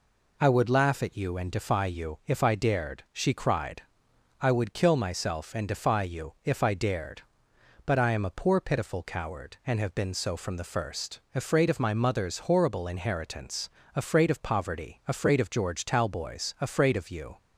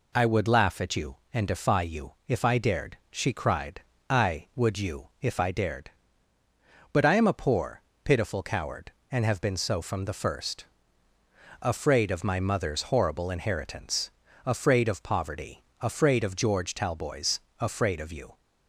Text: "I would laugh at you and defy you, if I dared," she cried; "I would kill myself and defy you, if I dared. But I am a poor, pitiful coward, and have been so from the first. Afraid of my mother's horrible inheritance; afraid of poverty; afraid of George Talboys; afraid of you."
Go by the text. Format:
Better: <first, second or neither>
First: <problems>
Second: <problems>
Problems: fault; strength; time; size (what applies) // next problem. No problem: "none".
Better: first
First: none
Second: skips "kill myself and defy"; at 4.7 s